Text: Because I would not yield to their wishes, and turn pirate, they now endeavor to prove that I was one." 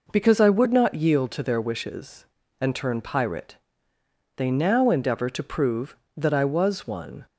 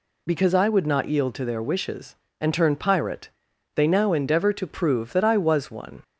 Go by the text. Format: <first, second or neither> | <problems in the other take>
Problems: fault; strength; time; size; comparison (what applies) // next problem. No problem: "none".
neither | none